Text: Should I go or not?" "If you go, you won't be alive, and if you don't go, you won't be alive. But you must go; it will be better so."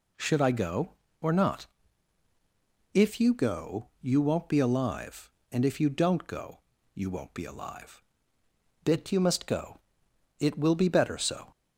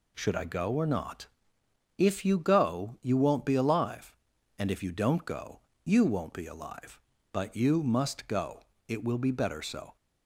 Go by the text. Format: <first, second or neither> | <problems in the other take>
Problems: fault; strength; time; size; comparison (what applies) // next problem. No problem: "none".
second | says "Bit" for "But"; at 8.8 s